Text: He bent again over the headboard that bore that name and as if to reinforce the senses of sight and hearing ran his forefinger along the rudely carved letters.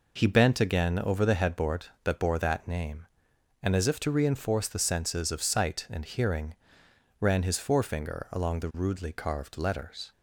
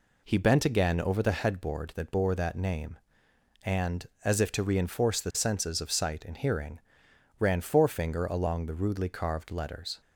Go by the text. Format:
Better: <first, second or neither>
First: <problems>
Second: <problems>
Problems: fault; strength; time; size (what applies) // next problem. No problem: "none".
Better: first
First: pauses between "hearing" and "ran"; noticeable; at 6.5 s; 0.66 s long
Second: pauses between "hearing" and "ran"; noticeable; at 6.8 s; 0.58 s long // skips "his"; at 7.6 s